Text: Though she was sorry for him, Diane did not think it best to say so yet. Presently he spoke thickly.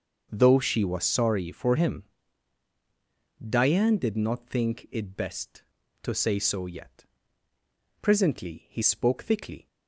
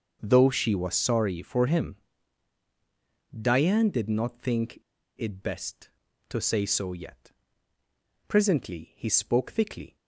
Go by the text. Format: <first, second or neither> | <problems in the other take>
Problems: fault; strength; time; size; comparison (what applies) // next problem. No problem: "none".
first | starts louder than the rest; until 1.2 s; 6 dB; noticeable in the first // pauses between "think" and "it"; at 4.7 s; 0.38 s long